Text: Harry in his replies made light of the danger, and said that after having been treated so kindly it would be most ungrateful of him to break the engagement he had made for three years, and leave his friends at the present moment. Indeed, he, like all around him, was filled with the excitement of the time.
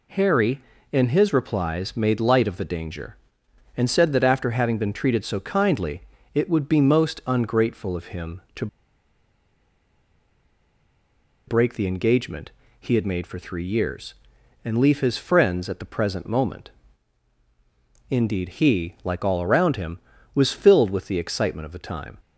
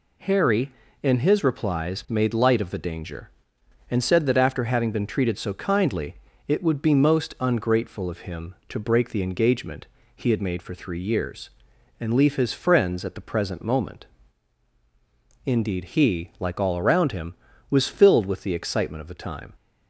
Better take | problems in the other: second | pauses between "kindly" and "it"; slight; at 6.0 s; 0.32 s long; slight in the second // pauses between "to" and "break"; strong; at 8.6 s; 2.8 s long // pauses between "engagement" and "he"; slight; at 12.5 s; 0.30 s long; slight in the second

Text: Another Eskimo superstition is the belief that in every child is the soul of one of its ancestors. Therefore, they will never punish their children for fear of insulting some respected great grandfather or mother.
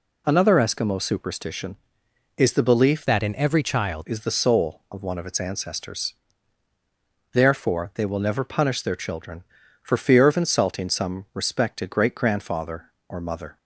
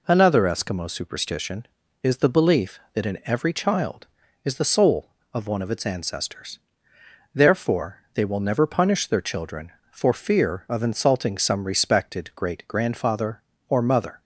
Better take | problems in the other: second | changes voice from "that" to "child"; from 3.0 to 4.0 s; 1.0 s long

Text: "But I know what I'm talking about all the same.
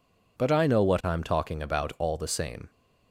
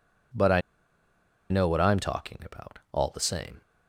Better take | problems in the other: first | pauses between "I" and "know"; noticeable; at 0.6 s; 0.89 s long

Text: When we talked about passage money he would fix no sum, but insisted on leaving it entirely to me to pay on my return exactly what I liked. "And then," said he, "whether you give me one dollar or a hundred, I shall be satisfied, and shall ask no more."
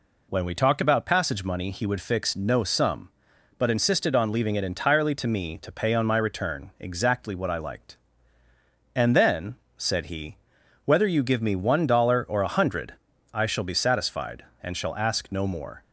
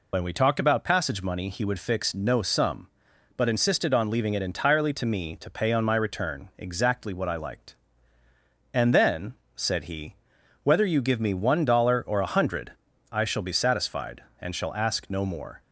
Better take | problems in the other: first | loses the start of "When"; at 0.1 s; 55 ms

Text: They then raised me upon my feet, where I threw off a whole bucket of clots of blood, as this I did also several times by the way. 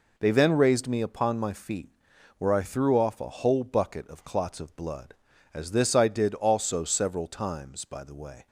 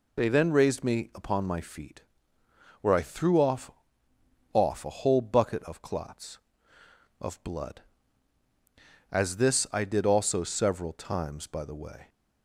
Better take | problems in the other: first | says "off" twice; at 4.5 s

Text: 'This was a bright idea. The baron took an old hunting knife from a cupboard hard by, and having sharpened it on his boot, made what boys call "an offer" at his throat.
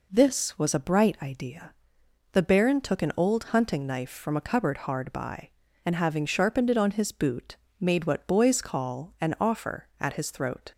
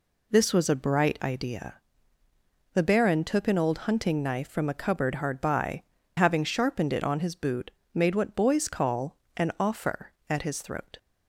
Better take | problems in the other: first | skips "and"; at 6.0 s // pauses between "call" and "an"; slight; at 9.1 s; 0.20 s long

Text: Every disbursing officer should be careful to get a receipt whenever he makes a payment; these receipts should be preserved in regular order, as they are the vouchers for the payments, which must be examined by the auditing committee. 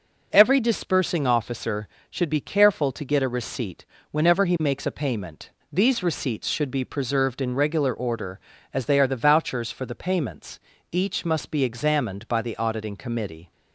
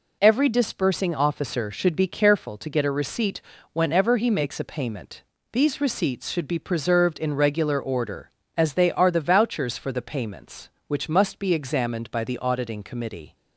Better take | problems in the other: second | pauses between "receipt" and "whenever"; slight; at 3.8 s; 0.28 s long; slight in the second // says "each" for "which"; at 10.8 s

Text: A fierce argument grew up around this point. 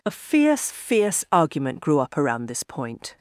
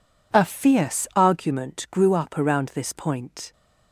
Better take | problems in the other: second | says "fierce" twice; at 0.7 s

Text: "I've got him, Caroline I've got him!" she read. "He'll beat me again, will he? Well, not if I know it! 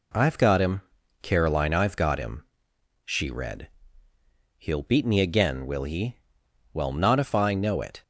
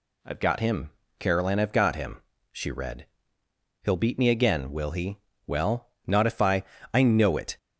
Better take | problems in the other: first | says "I" twice; at 6.9 s

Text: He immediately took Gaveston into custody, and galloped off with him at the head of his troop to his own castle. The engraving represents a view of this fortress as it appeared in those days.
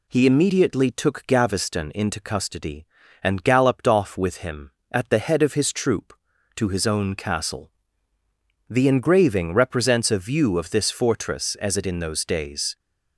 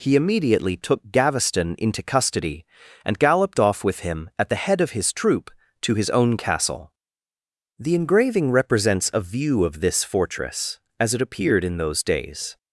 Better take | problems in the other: second | skips "appeared"; at 11.8 s

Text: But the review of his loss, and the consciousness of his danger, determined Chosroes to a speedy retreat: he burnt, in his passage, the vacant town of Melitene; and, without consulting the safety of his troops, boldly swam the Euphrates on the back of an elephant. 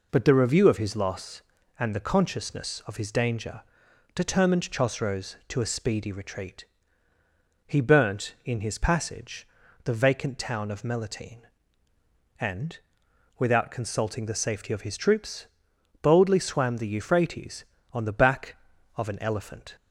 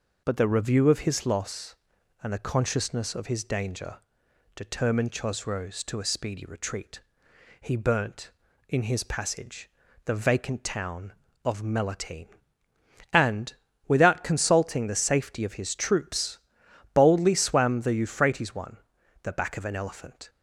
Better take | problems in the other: first | says "one" for "on"; at 18.5 s

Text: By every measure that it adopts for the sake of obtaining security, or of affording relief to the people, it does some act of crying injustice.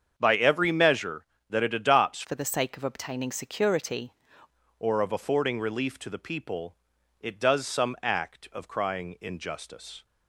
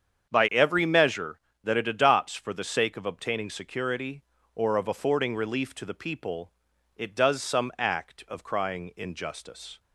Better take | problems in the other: second | starts louder than the rest; strong; until 1.1 s; 7.5 dB; strong in the second // changes voice from "for" to "security"; from 2.2 to 4.1 s; 1.9 s long

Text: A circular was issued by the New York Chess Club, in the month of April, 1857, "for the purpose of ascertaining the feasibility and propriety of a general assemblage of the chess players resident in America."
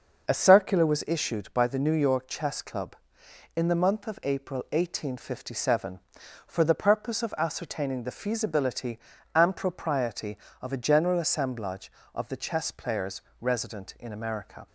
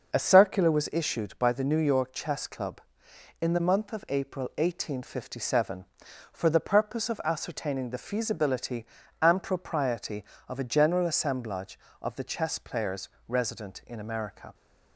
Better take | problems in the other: neither | starts louder than the rest; the same in both // pauses between "players" and "resident"; slight; the same in both

